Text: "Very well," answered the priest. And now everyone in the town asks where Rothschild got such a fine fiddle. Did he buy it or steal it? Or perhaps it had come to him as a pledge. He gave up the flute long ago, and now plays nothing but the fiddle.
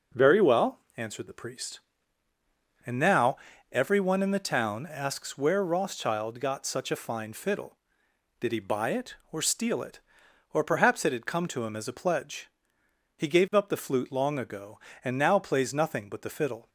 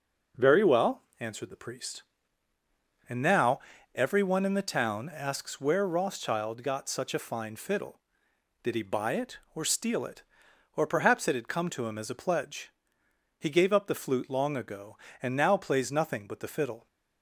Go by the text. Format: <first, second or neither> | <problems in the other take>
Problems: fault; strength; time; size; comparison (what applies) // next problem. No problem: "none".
neither | pauses between "now" and "everyone"; slight; the same in both